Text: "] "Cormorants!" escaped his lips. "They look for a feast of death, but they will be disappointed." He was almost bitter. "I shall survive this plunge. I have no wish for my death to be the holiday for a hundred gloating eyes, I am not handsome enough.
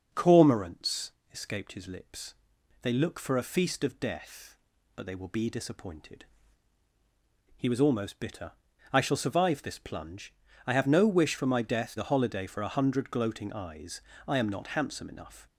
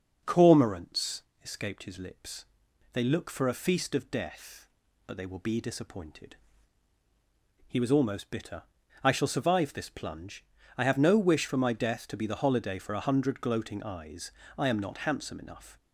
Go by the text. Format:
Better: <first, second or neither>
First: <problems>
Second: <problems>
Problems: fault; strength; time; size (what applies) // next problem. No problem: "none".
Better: second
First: starts louder than the rest; noticeable; until 1.3 s; 6 dB // skips "to be"; at 11.9 s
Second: starts louder than the rest; noticeable; until 1.4 s; 6 dB